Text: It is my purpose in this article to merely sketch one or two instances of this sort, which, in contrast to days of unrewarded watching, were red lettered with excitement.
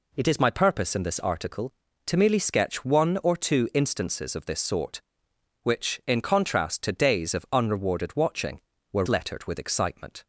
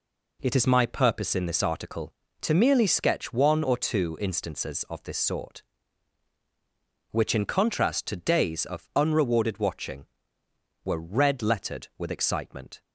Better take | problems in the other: second | skips "red"; at 9.0 s

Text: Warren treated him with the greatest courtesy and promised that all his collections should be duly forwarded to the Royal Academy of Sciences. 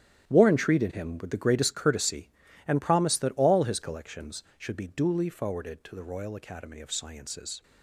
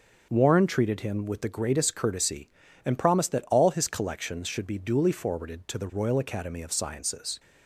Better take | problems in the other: second | gets quieter; strong; throughout; 13 dB // starts louder than the rest; strong; until 1.3 s; 11 dB; also in the second

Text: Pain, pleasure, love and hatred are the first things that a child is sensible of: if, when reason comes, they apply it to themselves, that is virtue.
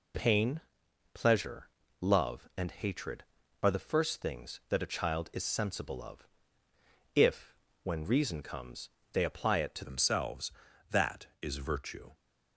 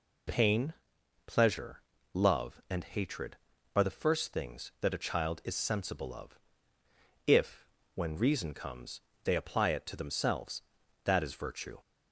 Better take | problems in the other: second | changes voice at "themselves"; from 9.8 s on; 2.3 s long

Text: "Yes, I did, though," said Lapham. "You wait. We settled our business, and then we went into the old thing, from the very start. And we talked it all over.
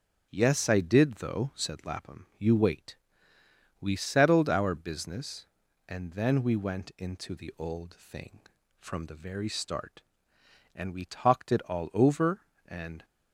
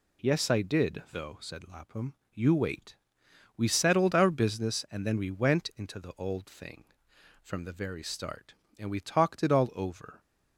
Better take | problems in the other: second | starts louder than the rest; strong; until 1.3 s; 7.5 dB // goes on to say "And"; slight; from 12.6 s on; 0.38 s long

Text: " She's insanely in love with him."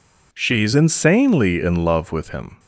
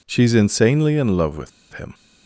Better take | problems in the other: first | pauses between "with" and "him"; slight; at 1.5 s; 0.23 s long

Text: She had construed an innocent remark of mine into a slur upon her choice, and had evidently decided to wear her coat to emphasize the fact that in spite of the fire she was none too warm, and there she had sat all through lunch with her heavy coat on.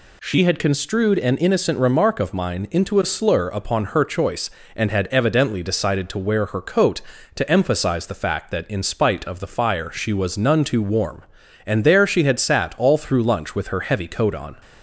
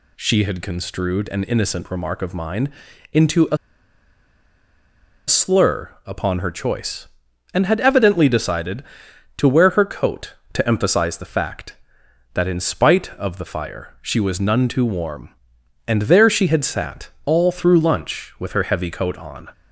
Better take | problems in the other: first | pauses between "mine" and "into"; at 2.7 s; 0.40 s long // pauses between "a" and "slur"; strong; at 3.5 s; 1.7 s long // pauses between "sat" and "all"; slight; at 17.0 s; 0.16 s long

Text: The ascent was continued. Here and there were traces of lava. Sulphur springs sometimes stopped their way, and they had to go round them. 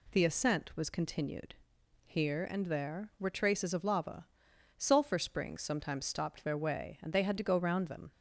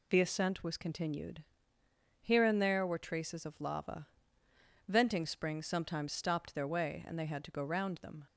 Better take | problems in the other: first | says "Venting" for "Sulphur"; at 4.8 s

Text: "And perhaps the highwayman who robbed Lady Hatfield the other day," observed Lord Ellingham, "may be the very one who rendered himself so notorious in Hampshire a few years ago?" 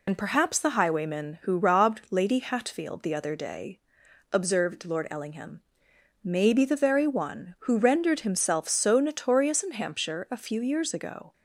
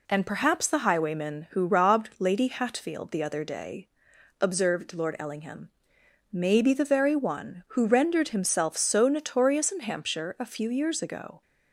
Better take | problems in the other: second | loses the start of "And"; at 0.0 s; 90 ms

